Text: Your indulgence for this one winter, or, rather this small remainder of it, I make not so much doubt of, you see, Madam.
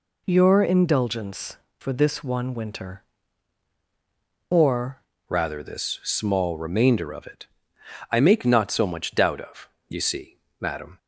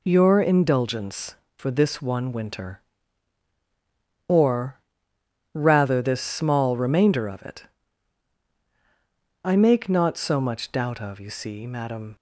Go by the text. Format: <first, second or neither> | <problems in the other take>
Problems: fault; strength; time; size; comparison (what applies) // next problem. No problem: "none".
second | changes voice at "rather"; from 5.2 s on; 5.7 s long